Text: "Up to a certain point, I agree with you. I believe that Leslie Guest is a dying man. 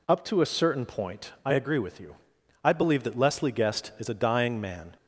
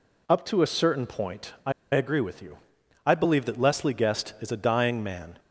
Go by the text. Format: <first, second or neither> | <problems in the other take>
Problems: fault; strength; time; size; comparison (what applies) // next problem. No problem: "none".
first | pauses between "I" and "agree"; slight; at 1.7 s; 0.22 s long